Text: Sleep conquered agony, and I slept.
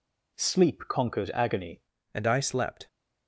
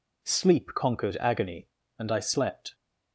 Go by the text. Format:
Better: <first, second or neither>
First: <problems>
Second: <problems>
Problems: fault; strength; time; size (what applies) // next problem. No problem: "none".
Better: second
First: changes voice at "and"; from 2.1 s on; 0.7 s long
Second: none